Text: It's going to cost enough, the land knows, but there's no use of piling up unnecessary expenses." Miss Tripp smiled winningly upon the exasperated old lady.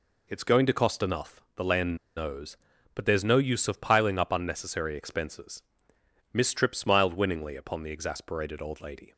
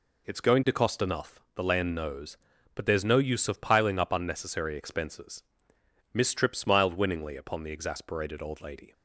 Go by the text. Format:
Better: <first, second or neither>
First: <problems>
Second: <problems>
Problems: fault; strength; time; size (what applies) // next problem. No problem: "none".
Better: second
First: pauses between "land" and "knows"; slight; at 1.9 s; 0.21 s long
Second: none